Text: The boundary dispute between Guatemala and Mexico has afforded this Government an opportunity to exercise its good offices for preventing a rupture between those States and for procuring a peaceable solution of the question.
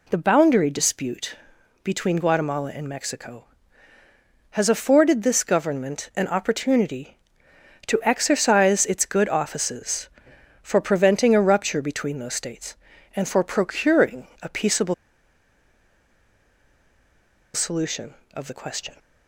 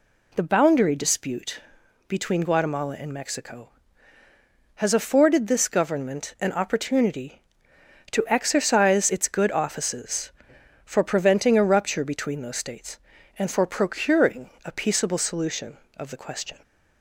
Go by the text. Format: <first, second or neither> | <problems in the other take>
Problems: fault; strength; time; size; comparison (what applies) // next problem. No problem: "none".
second | pauses between "dispute" and "between"; noticeable; at 1.3 s; 0.48 s long; noticeable in the second // pauses between "peaceable" and "solution"; strong; at 14.9 s; 2.5 s long